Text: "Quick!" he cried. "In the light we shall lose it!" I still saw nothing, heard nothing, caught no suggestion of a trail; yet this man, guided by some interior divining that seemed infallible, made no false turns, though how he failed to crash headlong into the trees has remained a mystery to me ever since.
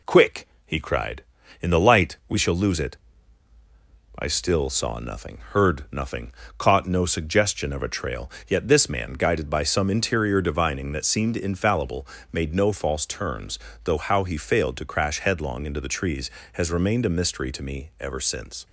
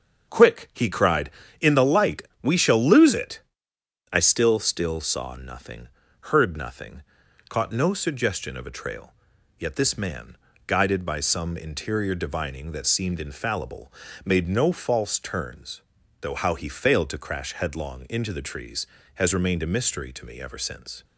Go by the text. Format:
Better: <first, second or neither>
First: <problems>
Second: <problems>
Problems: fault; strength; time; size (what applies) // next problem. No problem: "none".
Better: first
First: none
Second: starts louder than the rest; until 1.6 s; 6.5 dB // pauses between "light" and "we"; slight; at 2.2 s; 0.22 s long // says "still" twice; at 4.5 s